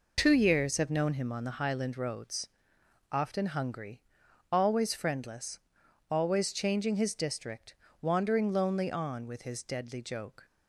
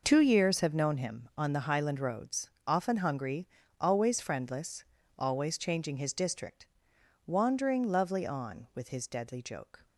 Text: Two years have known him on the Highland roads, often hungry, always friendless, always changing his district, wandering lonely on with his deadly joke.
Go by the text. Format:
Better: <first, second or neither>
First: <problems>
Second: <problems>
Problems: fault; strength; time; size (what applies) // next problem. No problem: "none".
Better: first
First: none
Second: says "lovely" for "lonely"; at 7.8 s